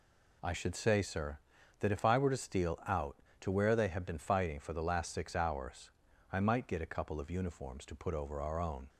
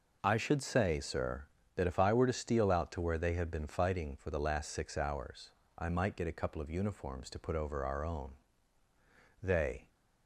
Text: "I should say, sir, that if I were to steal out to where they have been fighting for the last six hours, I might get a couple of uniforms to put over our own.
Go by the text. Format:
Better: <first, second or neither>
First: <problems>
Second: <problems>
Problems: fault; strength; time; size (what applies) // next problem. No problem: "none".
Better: first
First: none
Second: goes on to say "They"; slight; from 9.4 s on; 0.46 s long